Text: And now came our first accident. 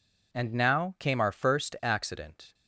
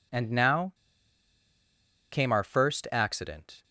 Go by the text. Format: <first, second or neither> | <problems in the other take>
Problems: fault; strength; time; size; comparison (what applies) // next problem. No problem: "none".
first | pauses between "now" and "came"; strong; at 0.7 s; 1.3 s long